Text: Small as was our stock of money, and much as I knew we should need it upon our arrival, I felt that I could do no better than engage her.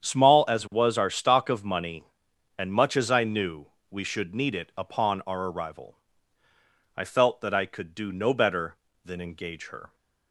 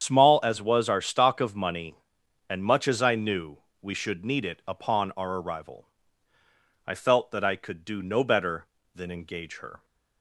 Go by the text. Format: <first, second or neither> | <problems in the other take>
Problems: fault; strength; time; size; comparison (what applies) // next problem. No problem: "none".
first | loses the start of "Small"; at 0.0 s; 35 ms // starts louder than the rest; strong; until 1.0 s; 8 dB; strong in the first // pauses between "knew" and "we"; slight; at 3.5 s; 0.20 s long; slight in the first